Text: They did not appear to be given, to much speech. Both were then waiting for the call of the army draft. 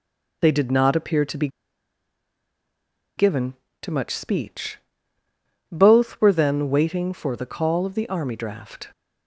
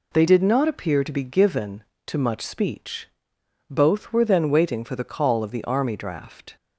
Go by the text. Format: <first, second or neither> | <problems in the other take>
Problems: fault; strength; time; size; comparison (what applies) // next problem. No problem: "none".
second | pauses between "be" and "given"; strong; at 1.4 s; 1.6 s long